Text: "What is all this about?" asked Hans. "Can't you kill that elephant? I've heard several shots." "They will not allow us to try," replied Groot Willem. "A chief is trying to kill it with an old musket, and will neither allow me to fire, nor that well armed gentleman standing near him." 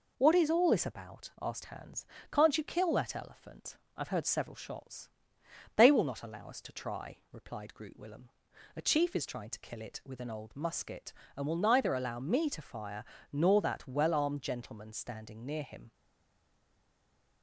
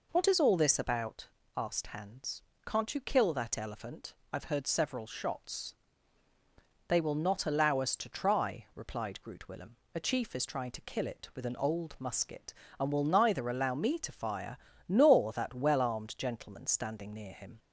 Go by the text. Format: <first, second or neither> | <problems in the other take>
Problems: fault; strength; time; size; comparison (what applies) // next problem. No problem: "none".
second | stays silent after the last word; noticeable; from 15.9 s on; 1.5 s long